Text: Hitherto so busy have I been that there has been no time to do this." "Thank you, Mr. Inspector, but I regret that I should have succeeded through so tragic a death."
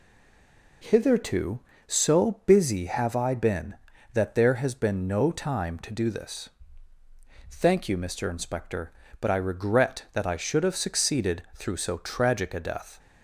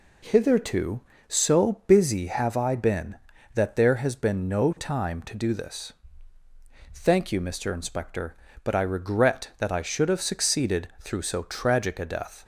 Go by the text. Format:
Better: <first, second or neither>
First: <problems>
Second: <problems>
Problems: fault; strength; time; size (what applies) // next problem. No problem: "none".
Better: second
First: stays silent before the first word; slight; until 0.8 s; 0.8 s long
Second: none